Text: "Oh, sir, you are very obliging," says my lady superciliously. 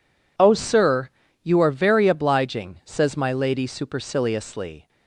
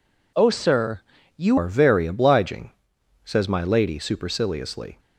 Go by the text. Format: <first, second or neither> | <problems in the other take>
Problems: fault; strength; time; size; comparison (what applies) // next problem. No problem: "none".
first | changes voice at "are"; from 1.5 s on; 3.4 s long